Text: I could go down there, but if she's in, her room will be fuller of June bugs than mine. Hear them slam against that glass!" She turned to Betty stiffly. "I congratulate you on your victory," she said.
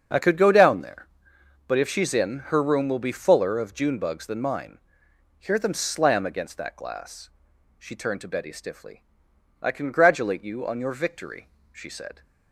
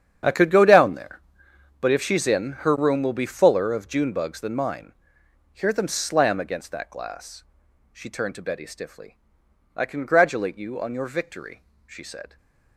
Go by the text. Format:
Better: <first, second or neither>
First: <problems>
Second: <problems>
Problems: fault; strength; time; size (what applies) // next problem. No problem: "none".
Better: first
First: starts louder than the rest; until 1.7 s; 7 dB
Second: gets quieter; strong; throughout; 15.5 dB // starts louder than the rest; strong; until 1.8 s; 8.5 dB // stays silent after the last word; slight; from 12.2 s on; 0.5 s long